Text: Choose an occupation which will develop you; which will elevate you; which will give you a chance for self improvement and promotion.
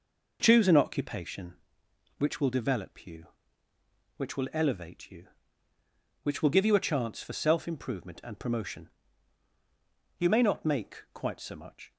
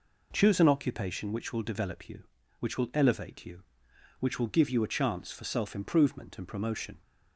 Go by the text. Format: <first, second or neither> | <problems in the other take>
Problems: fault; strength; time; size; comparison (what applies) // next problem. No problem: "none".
second | goes on to say "You may not make quite so much"; strong; from 10.1 s on; 1.7 s long